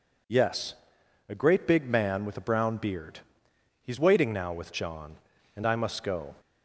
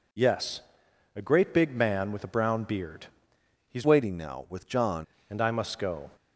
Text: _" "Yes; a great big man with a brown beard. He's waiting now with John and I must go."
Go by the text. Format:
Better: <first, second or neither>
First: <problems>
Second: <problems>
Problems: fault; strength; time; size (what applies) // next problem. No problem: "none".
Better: first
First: none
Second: changes voice from "waiting" to "John"; from 3.8 to 5.0 s; 1.2 s long